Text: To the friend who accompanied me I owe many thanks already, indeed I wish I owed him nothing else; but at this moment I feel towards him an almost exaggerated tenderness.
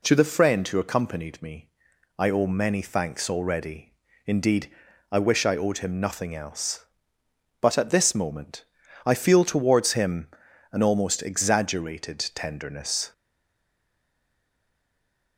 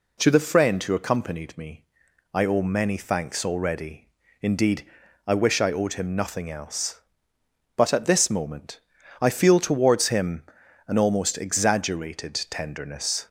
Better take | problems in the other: second | pauses between "me" and "I"; noticeable; at 1.6 s; 0.50 s long; noticeable in the second // pauses between "indeed" and "I"; at 4.6 s; 0.44 s long; also in the second // pauses between "moment" and "I"; at 8.6 s; 0.42 s long; also in the second // pauses between "him" and "an"; noticeable; at 10.2 s; 0.46 s long; noticeable in the second // pauses between "exaggerated" and "tenderness"; slight; at 12.1 s; 0.16 s long; slight in the second // stays silent after the last word; from 13.1 s on; 2.2 s long

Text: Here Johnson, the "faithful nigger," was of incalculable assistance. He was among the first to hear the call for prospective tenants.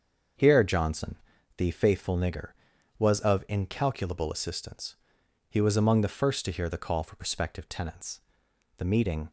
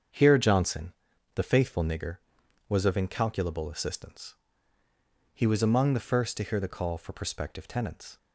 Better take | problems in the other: second | starts louder than the rest; until 1.7 s; 6.5 dB; strong in the second // goes on to say "The meeting"; from 8.7 s on; 0.54 s long

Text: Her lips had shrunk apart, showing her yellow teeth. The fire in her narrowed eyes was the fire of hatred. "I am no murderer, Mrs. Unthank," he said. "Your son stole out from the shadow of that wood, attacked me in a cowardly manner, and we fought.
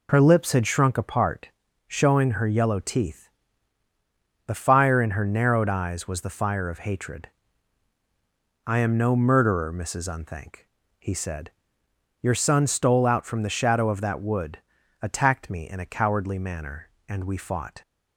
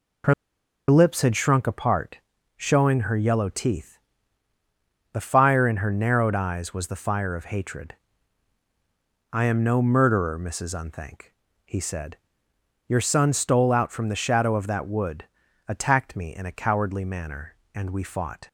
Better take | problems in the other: first | pauses between "Her" and "lips"; noticeable; at 0.3 s; 0.55 s long

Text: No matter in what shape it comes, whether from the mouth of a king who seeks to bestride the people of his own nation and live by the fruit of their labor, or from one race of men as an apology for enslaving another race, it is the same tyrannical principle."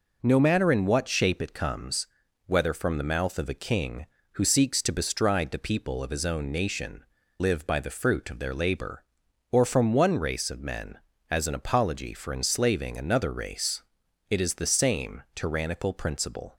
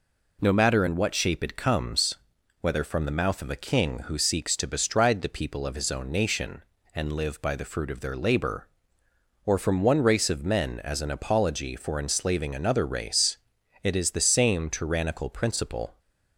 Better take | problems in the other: second | skips "and"; at 7.2 s

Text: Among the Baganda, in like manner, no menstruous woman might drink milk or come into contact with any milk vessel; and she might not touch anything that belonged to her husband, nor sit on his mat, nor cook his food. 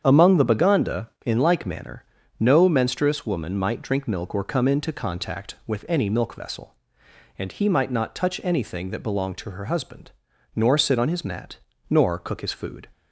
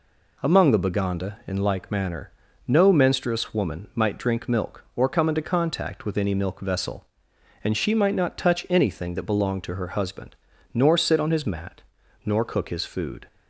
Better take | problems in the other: second | starts louder than the rest; strong; until 1.0 s; 8 dB // says "he" for "she"; at 7.4 s

